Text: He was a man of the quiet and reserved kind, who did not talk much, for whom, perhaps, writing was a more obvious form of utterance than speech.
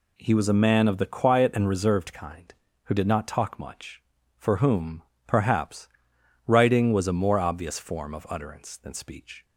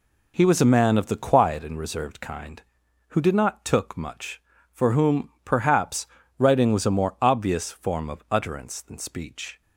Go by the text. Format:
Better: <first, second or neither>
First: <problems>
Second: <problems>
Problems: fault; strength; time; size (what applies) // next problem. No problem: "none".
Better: first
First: none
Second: says "took" for "talk"; at 3.6 s